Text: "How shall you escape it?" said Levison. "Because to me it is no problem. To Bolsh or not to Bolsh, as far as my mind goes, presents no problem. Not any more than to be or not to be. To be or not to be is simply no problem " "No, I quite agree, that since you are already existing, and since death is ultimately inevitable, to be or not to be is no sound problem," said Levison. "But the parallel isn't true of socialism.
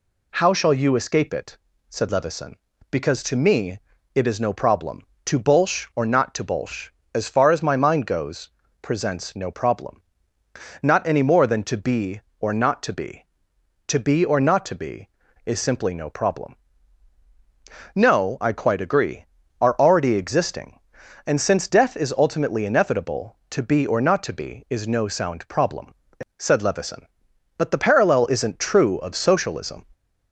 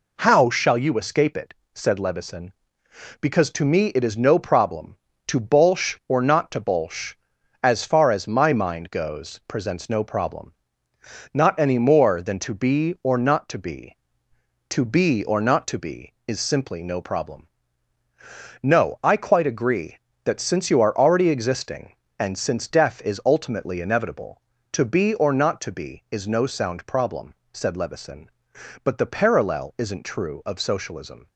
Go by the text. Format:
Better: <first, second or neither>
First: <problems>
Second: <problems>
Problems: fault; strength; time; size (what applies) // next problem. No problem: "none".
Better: second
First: pauses between "me" and "it"; slight; at 3.7 s; 0.34 s long // skips "that since you"; at 19.4 s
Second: none